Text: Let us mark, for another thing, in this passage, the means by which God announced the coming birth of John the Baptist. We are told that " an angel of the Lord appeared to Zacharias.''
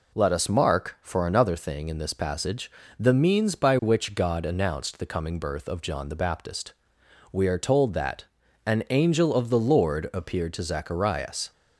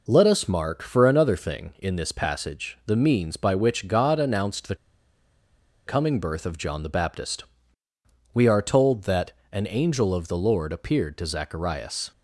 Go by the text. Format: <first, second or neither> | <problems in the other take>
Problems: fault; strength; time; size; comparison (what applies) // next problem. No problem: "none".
first | pauses between "the" and "coming"; at 4.7 s; 1.1 s long